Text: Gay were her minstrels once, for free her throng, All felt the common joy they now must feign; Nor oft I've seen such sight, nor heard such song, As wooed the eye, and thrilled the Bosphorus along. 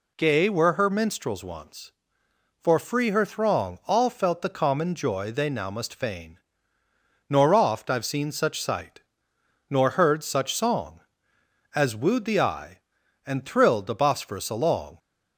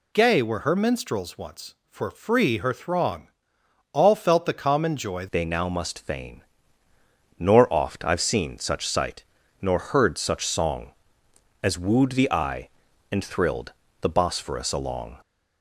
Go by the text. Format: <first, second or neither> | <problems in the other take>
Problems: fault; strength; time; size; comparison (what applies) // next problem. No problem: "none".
first | changes voice at "they"; from 5.3 s on; 9.8 s long // pauses between "thrilled" and "the"; slight; at 13.7 s; 0.26 s long